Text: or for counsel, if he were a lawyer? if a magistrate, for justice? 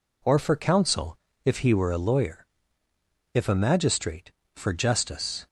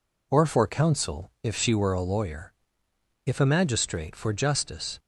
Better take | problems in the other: first | says "she" for "he"; at 1.5 s

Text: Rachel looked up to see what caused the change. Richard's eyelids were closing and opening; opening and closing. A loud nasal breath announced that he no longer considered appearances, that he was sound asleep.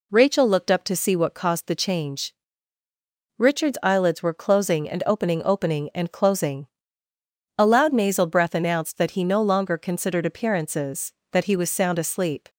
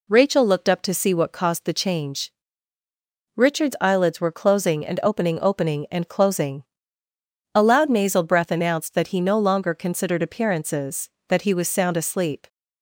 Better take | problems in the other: neither | none

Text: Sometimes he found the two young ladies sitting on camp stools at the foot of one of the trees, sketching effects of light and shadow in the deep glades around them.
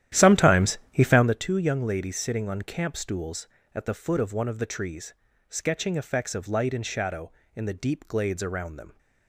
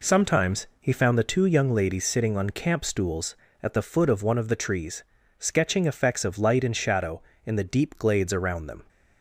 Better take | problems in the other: second | starts louder than the rest; strong; until 1.4 s; 12 dB

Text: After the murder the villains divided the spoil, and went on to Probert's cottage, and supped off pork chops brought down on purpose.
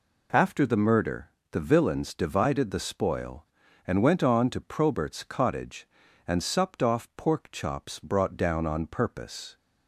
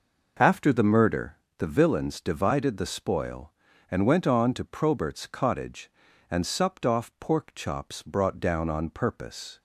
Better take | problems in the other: first | starts louder than the rest; noticeable; until 1.5 s; 5.5 dB // pauses between "murder" and "the"; slight; at 1.3 s; 0.22 s long; slight in the first

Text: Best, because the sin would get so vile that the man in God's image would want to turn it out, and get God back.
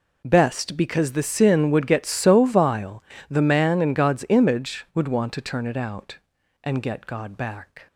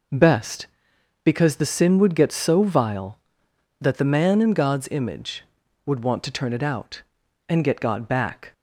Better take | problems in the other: second | skips "that"; at 3.1 s

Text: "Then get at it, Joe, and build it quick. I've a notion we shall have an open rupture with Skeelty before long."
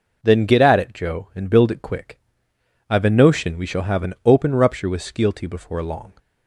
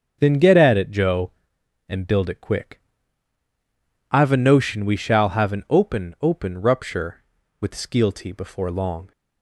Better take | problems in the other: first | starts louder than the rest; until 1.2 s; 6.5 dB // says "open" twice; at 6.1 s

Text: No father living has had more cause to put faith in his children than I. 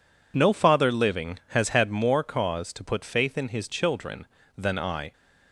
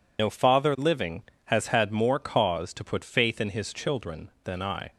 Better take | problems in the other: first | loses the start of "No"; at 0.1 s; 95 ms

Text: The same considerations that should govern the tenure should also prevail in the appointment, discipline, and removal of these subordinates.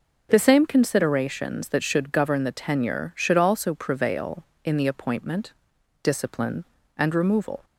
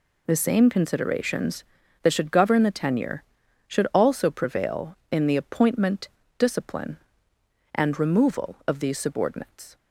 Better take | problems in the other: second | stops before "of these subordinates"; at 7.6 s

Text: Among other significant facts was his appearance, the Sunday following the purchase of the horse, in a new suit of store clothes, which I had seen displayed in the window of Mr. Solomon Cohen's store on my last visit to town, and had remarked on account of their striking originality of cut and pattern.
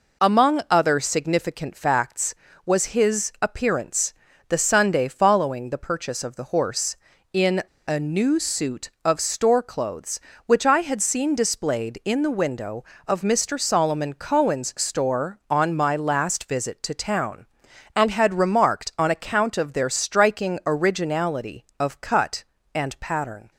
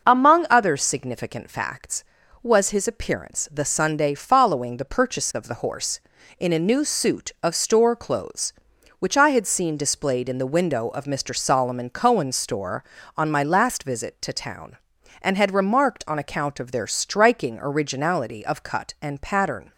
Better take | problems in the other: second | pauses between "in" and "a"; slight; at 7.6 s; 0.23 s long

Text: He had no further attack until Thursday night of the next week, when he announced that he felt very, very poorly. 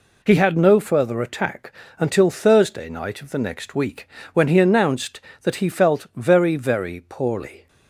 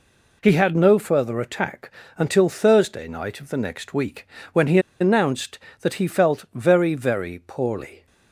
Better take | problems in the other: first | pauses between "attack" and "until"; slight; at 1.9 s; 0.26 s long; slight in the first // pauses between "he" and "announced"; slight; at 4.7 s; 0.21 s long

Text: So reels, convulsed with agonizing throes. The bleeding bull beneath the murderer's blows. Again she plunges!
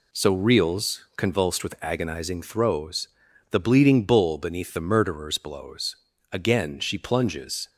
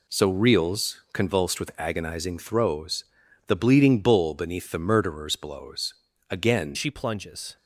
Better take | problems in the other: first | changes voice at "she"; from 6.7 s on; 0.8 s long

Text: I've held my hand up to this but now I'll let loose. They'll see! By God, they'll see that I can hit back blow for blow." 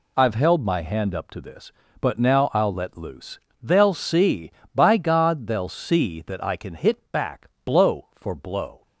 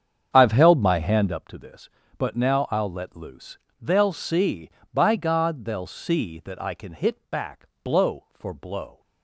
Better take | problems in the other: first | starts louder than the rest; strong; until 1.4 s; 7.5 dB // pauses between "back" and "blow"; slight; at 7.6 s; 0.16 s long; slight in the first

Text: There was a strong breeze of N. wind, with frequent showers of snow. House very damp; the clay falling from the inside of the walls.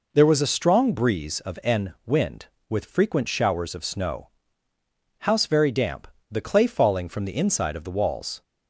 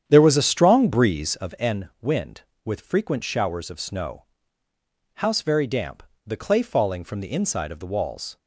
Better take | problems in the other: first | starts louder than the rest; strong; until 1.6 s; 9 dB

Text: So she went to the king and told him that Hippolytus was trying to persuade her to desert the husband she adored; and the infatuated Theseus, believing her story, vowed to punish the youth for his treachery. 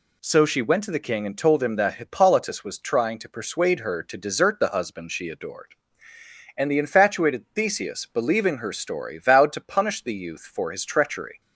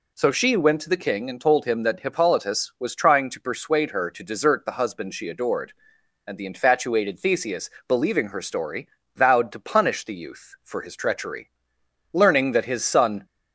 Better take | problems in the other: first | goes on to say "Learning that his son"; noticeable; from 12.1 s on; 1.1 s long

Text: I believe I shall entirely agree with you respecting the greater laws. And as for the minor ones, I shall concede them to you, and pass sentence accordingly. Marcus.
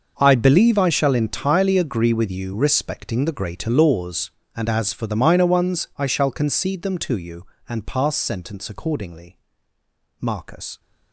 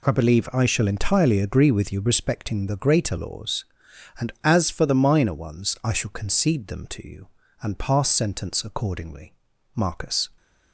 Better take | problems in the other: second | gets quieter; strong; throughout; 15.5 dB

